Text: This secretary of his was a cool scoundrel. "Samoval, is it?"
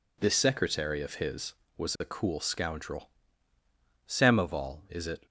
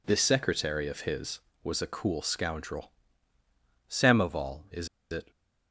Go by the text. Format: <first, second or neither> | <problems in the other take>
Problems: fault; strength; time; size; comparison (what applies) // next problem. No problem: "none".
first | pauses between "is" and "it"; slight; at 4.8 s; 0.23 s long